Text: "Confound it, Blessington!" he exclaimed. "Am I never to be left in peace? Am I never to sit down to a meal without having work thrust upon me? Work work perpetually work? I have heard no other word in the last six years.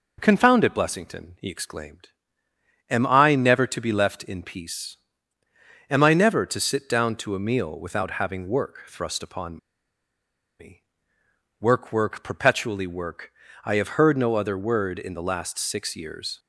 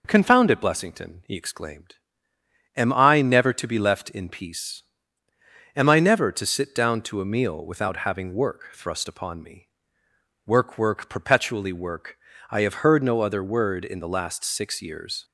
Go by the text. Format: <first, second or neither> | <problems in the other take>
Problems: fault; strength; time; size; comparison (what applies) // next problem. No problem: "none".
second | pauses between "upon" and "me"; at 9.5 s; 1.0 s long